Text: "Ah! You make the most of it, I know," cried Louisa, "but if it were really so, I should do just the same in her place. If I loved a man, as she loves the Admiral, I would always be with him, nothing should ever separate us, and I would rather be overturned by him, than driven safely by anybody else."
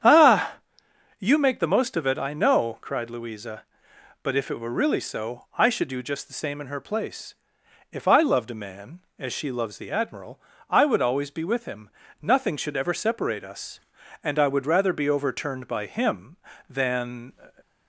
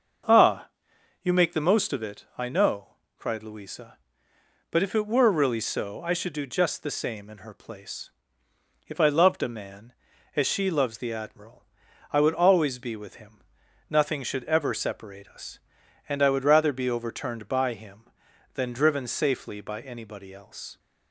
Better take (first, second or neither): second